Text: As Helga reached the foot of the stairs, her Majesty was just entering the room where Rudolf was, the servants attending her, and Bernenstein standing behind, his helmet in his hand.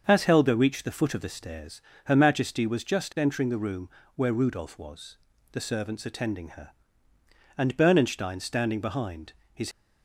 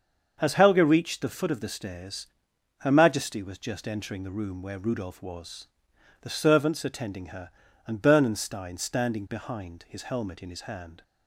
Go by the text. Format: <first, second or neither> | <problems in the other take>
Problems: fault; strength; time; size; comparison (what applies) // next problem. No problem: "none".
second | starts louder than the rest; until 1.0 s; 6.5 dB; also in the second // pauses between "room" and "where"; slight; at 3.8 s; 0.26 s long // stops before "helmet in his hand"; at 9.7 s